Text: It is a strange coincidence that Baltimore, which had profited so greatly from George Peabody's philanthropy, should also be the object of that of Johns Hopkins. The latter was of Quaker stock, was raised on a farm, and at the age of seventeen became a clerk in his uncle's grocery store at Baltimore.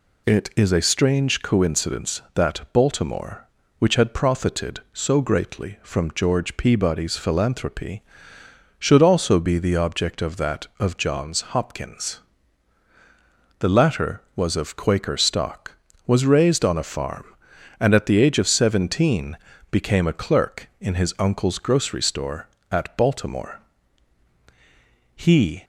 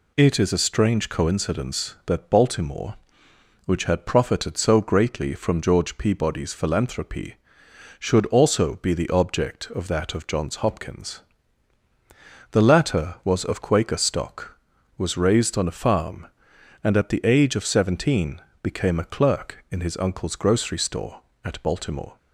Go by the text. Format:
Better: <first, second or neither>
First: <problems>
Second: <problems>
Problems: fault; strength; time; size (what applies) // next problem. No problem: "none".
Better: second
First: pauses between "seventeen" and "became"; slight; at 19.3 s; 0.34 s long // goes on to say "He"; from 25.1 s on; 0.50 s long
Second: pauses between "seventeen" and "became"; slight; at 18.3 s; 0.22 s long